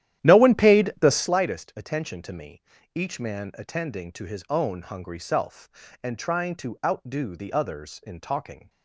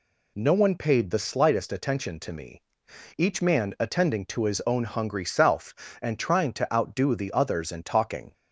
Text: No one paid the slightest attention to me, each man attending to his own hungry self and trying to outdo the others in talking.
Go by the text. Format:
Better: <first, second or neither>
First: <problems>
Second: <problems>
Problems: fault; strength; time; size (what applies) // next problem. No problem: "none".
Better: second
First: starts louder than the rest; strong; until 1.4 s; 12 dB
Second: none